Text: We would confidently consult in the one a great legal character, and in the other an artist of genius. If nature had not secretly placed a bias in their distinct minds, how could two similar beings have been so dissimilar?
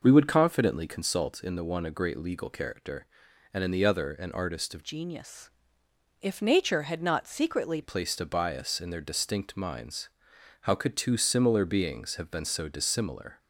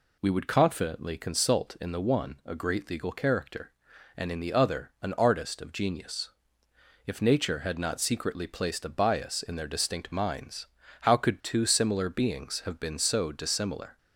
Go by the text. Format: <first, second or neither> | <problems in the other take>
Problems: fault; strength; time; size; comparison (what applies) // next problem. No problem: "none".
second | changes voice from "genius" to "secretly"; from 4.8 to 7.8 s; 3.0 s long